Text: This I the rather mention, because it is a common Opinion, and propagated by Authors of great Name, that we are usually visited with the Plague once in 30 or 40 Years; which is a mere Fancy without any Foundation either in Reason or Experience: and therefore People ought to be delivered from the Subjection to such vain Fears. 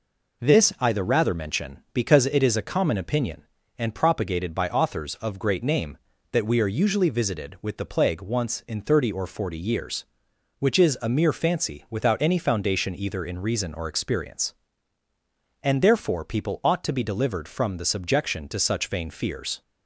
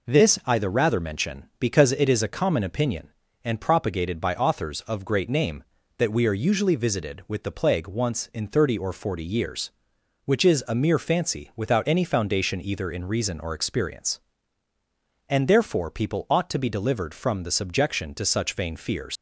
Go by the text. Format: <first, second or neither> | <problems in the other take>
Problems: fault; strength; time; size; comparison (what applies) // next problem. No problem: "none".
first | leaves "Fears" unfinished; at 19.1 s; 120 ms